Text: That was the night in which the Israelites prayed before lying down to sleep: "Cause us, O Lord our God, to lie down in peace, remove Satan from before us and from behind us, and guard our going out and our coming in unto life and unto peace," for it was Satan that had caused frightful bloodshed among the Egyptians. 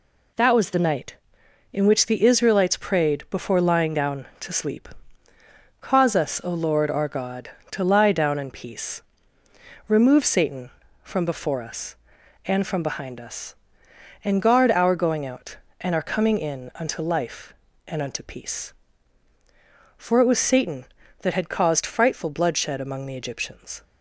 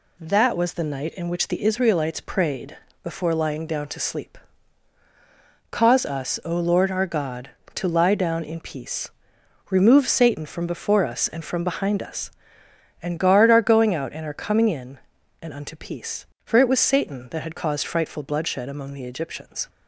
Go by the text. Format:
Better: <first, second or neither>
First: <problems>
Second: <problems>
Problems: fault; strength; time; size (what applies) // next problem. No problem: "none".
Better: first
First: none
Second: pauses between "prayed" and "before"; slight; at 2.7 s; 0.28 s long // skips "unto life"; at 15.1 s